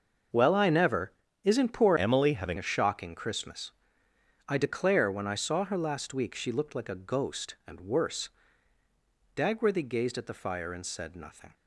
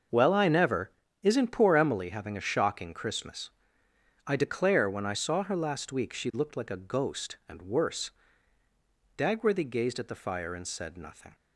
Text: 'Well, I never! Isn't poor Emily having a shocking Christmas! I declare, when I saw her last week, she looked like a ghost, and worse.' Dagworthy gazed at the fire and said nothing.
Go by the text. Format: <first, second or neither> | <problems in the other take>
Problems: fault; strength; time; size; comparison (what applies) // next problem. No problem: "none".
second | starts louder than the rest; until 1.6 s; 6.5 dB; also in the second // changes voice from "Emily" to "having"; from 1.9 to 2.5 s; 0.6 s long